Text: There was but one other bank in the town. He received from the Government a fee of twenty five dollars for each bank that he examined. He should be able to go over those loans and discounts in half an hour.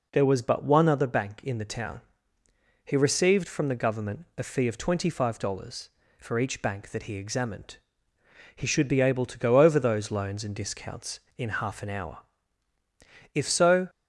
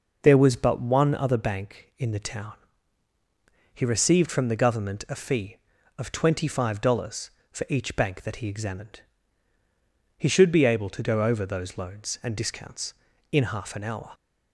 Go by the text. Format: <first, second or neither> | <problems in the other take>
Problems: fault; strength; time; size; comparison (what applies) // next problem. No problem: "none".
second | goes on to say "If so"; from 13.3 s on; 0.56 s long